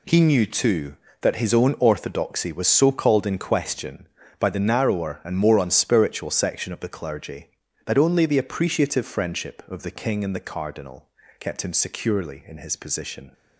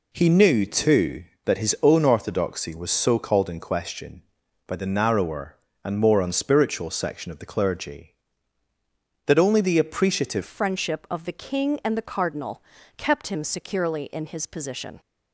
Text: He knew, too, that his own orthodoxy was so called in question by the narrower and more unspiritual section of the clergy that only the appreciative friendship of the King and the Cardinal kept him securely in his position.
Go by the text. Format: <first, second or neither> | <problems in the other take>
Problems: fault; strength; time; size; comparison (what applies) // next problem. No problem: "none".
first | changes voice at "friendship"; from 10.4 s on; 4.5 s long // pauses between "Cardinal" and "kept"; slight; at 12.6 s; 0.36 s long; slight in the first